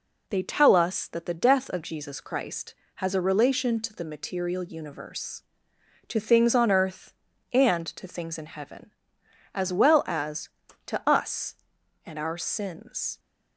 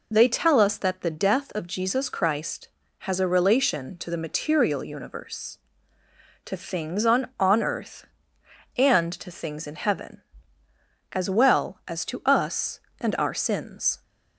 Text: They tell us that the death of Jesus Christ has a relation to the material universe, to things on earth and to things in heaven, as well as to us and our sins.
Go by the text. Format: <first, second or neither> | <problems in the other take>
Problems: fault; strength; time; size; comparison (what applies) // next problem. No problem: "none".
first | says "on" twice; at 7.4 s